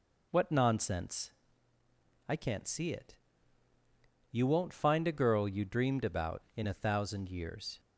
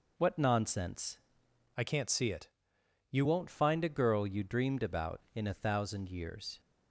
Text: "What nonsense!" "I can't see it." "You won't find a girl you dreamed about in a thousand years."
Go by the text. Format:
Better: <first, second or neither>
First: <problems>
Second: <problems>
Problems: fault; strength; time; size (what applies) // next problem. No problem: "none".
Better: first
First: none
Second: changes voice from "I" to "You"; from 1.7 to 3.2 s; 1.5 s long